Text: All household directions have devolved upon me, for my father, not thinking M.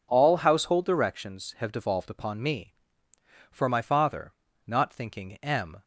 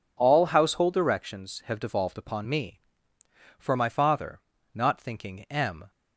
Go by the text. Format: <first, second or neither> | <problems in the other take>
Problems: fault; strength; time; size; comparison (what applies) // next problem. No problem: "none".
neither | none